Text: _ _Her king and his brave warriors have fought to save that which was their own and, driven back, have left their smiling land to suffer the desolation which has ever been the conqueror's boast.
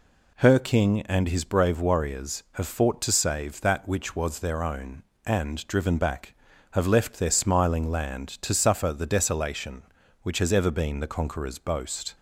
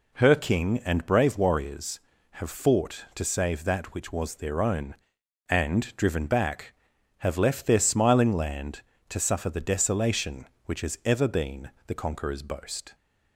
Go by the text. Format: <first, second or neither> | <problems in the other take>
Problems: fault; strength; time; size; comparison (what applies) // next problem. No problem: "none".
first | skips "his"; at 1.0 s // pauses between "been" and "the"; slight; at 11.7 s; 0.16 s long